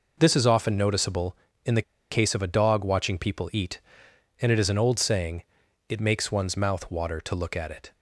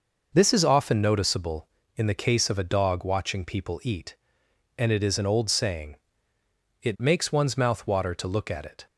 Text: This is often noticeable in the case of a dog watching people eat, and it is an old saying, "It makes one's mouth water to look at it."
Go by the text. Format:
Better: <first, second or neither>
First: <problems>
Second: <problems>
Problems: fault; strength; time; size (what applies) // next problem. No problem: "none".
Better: second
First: pauses between "the" and "case"; slight; at 1.8 s; 0.29 s long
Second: none